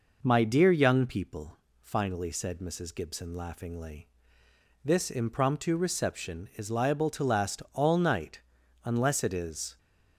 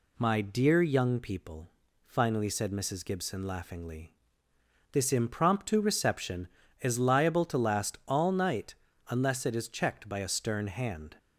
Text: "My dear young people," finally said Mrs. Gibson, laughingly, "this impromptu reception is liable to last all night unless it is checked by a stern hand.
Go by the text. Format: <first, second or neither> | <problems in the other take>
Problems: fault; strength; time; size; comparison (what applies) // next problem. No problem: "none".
second | pauses between "night" and "unless"; at 8.4 s; 0.42 s long; slight in the second // stops before "checked by a stern hand"; at 9.7 s